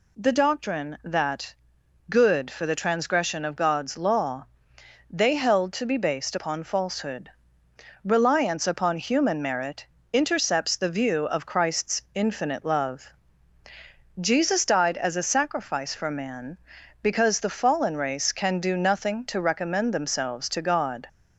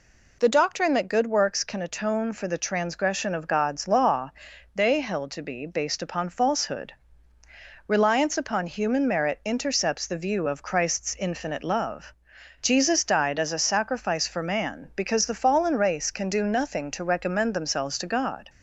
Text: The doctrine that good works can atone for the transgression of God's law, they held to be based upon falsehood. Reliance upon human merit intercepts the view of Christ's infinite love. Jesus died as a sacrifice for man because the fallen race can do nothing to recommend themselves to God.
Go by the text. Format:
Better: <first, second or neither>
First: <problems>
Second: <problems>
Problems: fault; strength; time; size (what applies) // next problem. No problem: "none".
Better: second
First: pauses between "that" and "good"; noticeable; at 1.5 s; 0.56 s long // skips "works can atone"; at 2.4 s // pauses between "merit" and "intercepts"; slight; at 9.8 s; 0.26 s long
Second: none